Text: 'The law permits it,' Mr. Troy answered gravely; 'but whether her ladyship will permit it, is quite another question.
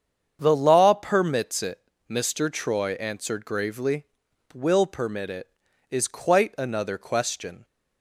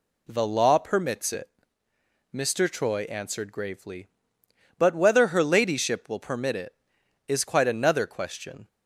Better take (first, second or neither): second